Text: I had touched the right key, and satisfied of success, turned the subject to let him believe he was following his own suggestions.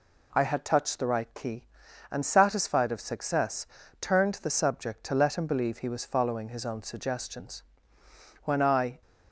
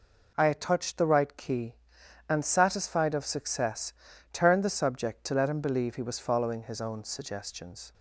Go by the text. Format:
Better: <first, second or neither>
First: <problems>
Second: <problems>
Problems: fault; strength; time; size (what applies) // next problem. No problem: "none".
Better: second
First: goes on to say "When I"; from 8.4 s on; 0.56 s long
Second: none